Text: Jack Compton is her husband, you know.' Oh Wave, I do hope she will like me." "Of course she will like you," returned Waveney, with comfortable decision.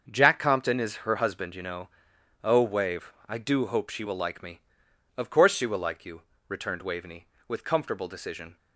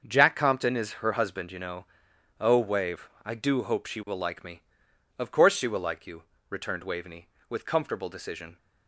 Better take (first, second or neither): neither